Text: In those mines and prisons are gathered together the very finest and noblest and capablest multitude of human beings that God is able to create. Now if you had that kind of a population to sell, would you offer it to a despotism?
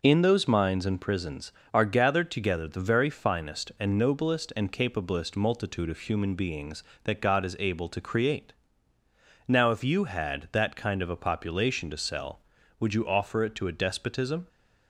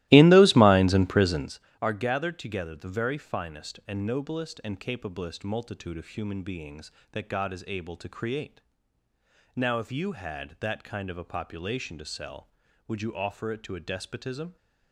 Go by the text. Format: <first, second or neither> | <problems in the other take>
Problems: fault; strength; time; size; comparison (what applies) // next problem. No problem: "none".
first | starts louder than the rest; strong; until 1.6 s; 17.5 dB